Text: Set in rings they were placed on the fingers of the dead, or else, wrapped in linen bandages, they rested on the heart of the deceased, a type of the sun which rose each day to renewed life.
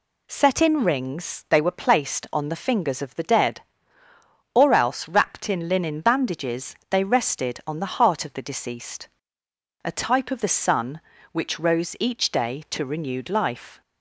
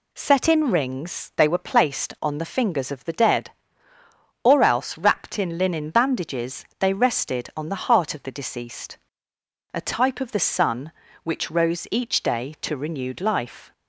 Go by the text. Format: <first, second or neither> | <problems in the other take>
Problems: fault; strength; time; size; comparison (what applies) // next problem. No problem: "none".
neither | none